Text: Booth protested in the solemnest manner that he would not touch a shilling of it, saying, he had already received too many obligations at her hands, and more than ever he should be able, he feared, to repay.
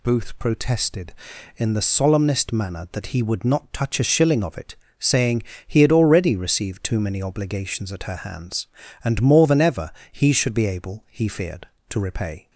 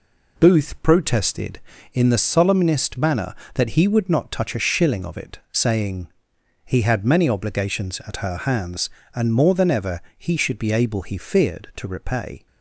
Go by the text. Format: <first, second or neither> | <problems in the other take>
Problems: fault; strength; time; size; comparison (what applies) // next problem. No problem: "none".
first | skips "already received too"; at 7.0 s // pauses between "ever" and "he"; slight; at 9.9 s; 0.18 s long; slight in the first